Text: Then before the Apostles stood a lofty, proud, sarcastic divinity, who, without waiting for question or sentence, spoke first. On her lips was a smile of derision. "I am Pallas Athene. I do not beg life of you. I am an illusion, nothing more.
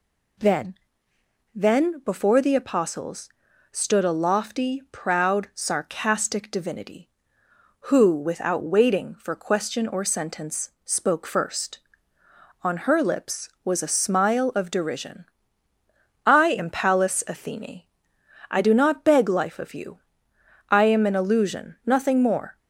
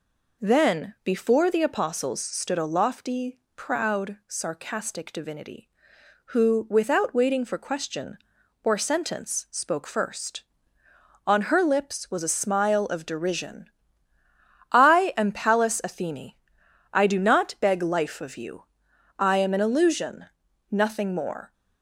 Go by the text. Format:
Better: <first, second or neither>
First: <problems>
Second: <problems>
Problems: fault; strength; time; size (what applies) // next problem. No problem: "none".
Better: second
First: says "Then" twice; at 1.5 s // pauses between "Apostles" and "stood"; at 3.2 s; 0.42 s long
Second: none